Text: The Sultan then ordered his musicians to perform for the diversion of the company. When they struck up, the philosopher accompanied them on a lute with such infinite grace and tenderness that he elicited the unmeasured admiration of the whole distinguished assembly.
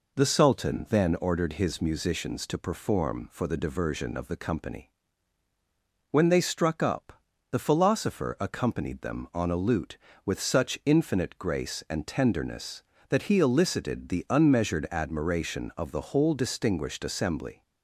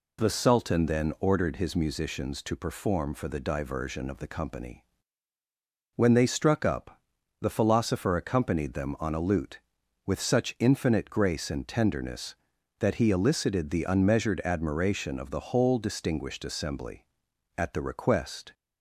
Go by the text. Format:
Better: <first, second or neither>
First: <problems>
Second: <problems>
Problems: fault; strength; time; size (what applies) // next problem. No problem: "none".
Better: first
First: none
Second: goes on to say "At the request"; noticeable; from 17.5 s on; 0.98 s long